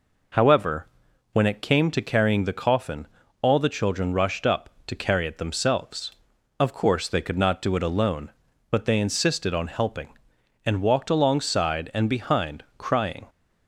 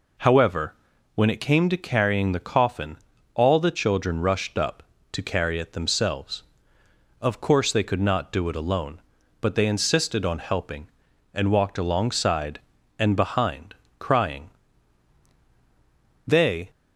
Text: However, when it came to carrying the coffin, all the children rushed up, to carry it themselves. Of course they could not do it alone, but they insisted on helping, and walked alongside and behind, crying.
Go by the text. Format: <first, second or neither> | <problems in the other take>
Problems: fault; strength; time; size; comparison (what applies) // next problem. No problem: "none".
first | goes on to say "They"; slight; from 16.2 s on; 0.44 s long